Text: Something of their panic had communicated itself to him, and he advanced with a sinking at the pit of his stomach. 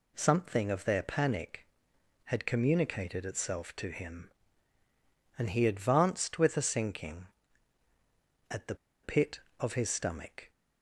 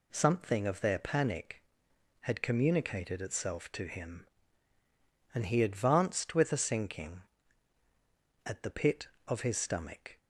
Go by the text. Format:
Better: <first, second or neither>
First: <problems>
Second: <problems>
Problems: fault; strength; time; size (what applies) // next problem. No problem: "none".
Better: second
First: pauses between "the" and "pit"; slight; at 8.7 s; 0.28 s long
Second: none